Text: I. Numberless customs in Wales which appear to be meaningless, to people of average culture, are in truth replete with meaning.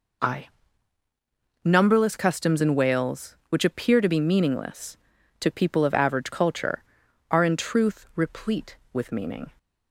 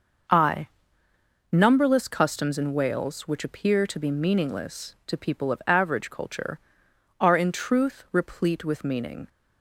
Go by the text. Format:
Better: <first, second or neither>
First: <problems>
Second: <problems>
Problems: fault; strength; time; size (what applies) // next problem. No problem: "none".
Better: neither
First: none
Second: none